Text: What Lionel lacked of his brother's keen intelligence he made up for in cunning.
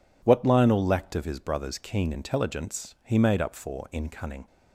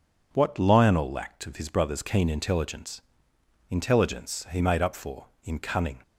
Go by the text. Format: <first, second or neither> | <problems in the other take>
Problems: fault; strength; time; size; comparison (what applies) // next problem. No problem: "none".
first | says "intelligence" twice; at 3.7 s